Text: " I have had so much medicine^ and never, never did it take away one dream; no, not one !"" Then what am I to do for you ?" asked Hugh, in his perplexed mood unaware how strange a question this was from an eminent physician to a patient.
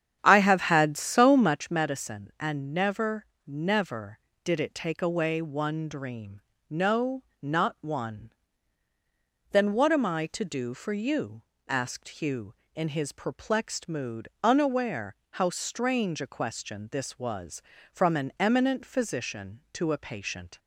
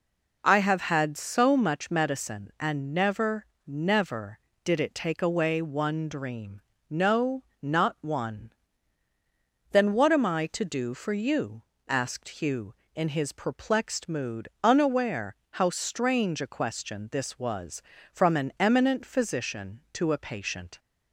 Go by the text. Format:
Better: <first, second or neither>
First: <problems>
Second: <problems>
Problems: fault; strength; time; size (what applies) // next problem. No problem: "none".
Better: second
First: starts louder than the rest; strong; until 1.8 s; 10 dB // pauses between "mood" and "unaware"; slight; at 14.2 s; 0.16 s long // pauses between "unaware" and "how"; slight; at 15.1 s; 0.20 s long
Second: pauses between "mood" and "unaware"; slight; at 14.4 s; 0.16 s long // pauses between "unaware" and "how"; slight; at 15.3 s; 0.20 s long